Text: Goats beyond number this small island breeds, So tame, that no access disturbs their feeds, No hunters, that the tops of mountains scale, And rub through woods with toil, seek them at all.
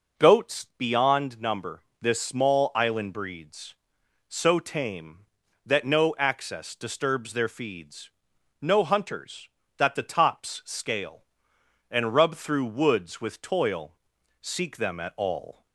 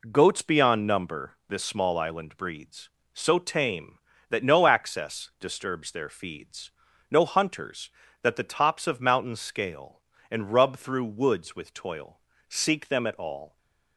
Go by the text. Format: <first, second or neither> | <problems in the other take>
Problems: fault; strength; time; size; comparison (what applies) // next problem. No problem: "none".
second | pauses between "number" and "this"; slight; at 1.8 s; 0.18 s long; slight in the second // skips "of mountains"; at 10.6 s